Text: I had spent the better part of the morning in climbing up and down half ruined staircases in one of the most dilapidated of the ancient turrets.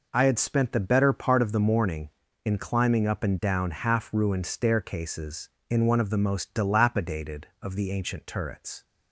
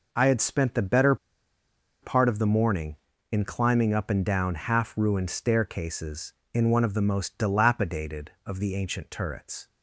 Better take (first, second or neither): first